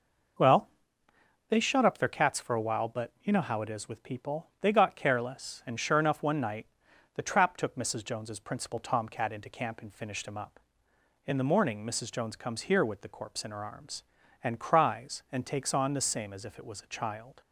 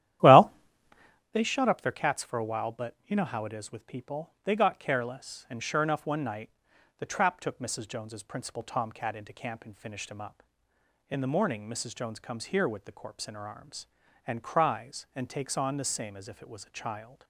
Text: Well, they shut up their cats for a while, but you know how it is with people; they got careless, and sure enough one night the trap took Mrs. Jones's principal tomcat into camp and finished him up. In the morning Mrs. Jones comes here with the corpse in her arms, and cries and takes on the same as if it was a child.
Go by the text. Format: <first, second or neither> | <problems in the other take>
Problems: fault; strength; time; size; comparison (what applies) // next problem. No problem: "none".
first | starts louder than the rest; strong; until 1.3 s; 12 dB // pauses between "night" and "the"; noticeable; at 6.4 s; 0.48 s long; noticeable in the first